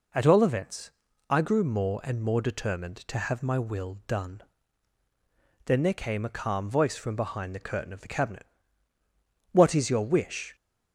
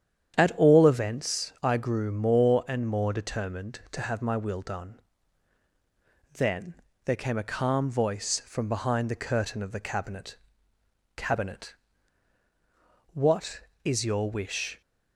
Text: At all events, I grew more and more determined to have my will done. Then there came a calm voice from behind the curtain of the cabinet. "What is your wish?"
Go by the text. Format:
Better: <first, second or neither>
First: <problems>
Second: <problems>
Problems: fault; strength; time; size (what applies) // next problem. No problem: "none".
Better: first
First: none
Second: starts louder than the rest; strong; until 1.4 s; 9 dB // pauses between "Then" and "there"; slight; at 6.7 s; 0.30 s long // says "cabinet" twice; at 11.1 s